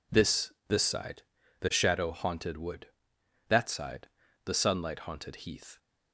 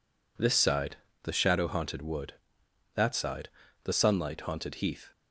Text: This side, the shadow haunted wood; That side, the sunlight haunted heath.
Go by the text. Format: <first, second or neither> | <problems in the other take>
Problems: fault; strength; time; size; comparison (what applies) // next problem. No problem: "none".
second | says "This" twice; at 0.6 s